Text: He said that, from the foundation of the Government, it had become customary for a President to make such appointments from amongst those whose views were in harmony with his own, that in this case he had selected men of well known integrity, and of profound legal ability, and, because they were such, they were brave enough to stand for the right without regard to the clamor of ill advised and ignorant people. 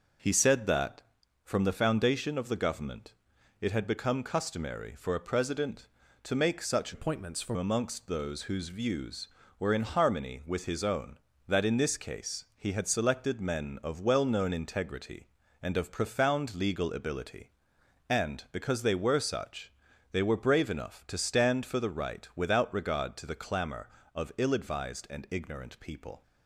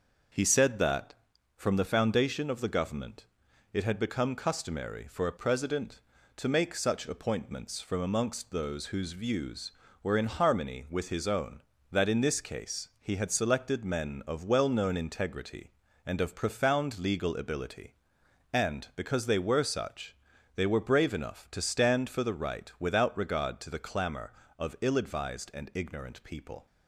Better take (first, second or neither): second